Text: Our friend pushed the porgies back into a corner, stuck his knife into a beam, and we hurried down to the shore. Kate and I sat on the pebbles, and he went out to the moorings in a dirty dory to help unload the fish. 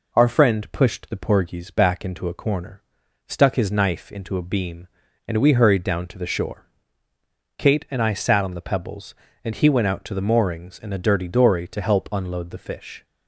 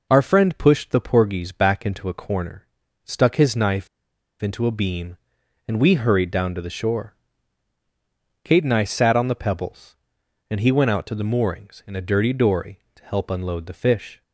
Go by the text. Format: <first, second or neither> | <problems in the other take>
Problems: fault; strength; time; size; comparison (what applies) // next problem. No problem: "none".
first | pauses between "knife" and "into"; noticeable; at 3.8 s; 0.53 s long